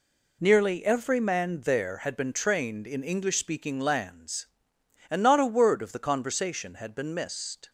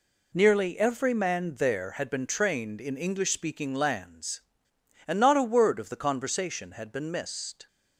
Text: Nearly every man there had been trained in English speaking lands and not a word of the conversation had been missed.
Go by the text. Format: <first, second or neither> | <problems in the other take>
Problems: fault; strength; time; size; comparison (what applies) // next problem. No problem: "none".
neither | none